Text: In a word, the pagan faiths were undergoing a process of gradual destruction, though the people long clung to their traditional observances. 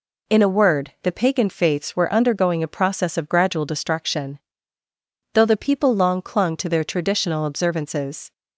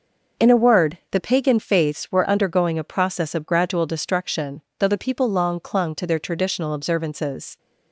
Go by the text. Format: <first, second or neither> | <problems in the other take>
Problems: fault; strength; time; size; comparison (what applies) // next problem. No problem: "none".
neither | none